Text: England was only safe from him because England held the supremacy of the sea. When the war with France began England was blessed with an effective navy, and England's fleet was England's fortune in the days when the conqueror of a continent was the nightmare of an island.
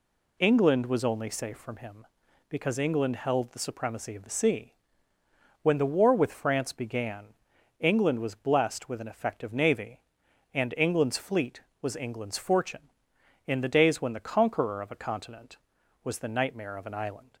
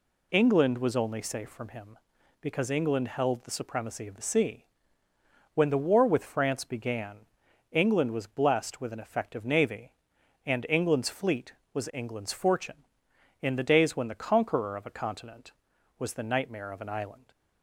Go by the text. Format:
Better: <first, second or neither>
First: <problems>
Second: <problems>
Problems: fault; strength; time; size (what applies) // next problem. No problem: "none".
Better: neither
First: pauses between "began" and "England"; noticeable; at 7.2 s; 0.52 s long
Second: pauses between "began" and "England"; noticeable; at 7.1 s; 0.52 s long